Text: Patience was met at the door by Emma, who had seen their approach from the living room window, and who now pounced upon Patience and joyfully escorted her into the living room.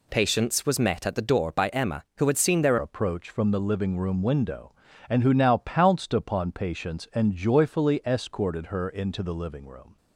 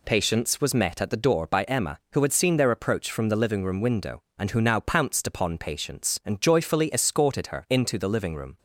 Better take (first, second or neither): second